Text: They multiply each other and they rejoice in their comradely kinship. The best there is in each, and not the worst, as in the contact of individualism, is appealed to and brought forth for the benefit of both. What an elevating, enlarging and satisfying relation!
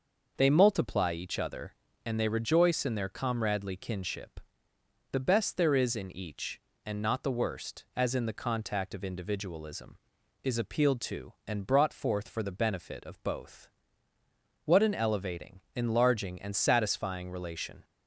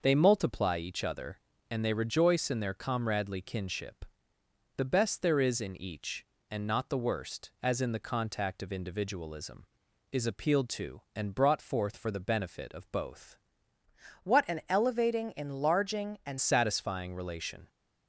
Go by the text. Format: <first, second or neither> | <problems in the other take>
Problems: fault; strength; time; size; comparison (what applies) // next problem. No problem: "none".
first | changes voice from "What" to "and"; from 14.2 to 16.3 s; 2.1 s long